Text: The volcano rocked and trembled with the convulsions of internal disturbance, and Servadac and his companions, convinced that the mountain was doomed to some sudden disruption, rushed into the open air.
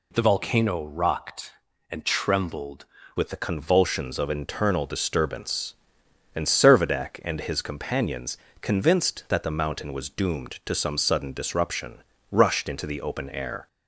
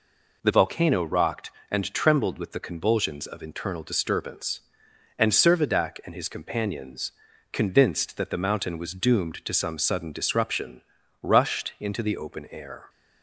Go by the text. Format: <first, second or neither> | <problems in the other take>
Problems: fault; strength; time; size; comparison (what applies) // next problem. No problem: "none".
second | changes voice at "with"; from 3.1 s on; 10.5 s long